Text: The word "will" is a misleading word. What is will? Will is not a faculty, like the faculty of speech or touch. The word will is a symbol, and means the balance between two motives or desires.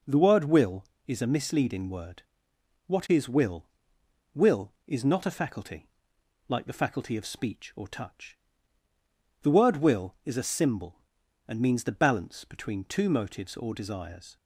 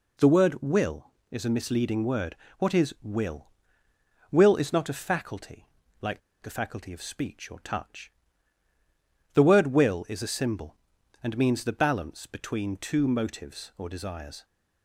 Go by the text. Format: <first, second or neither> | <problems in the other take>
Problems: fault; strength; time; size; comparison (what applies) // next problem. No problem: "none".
first | pauses between "like" and "the"; slight; at 6.1 s; 0.22 s long